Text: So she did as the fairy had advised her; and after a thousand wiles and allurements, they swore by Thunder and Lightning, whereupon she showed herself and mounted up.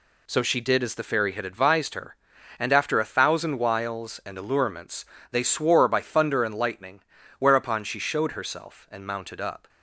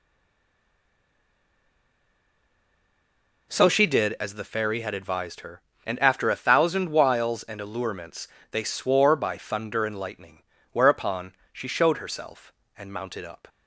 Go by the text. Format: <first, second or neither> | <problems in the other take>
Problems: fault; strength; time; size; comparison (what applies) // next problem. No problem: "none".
first | stays silent before the first word; strong; until 3.4 s; 3.4 s long // pauses between "whereupon" and "she"; slight; at 11.3 s; 0.18 s long